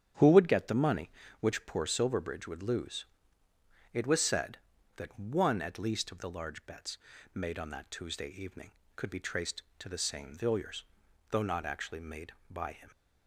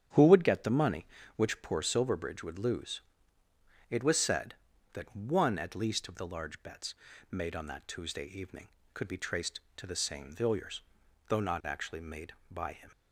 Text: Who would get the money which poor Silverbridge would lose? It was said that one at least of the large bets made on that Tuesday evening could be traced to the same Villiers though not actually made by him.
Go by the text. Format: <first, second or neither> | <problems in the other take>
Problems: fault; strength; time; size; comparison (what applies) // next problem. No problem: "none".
neither | starts louder than the rest; strong; the same in both // pauses between "bets" and "made"; slight; the same in both // pauses between "Villiers" and "though"; noticeable; the same in both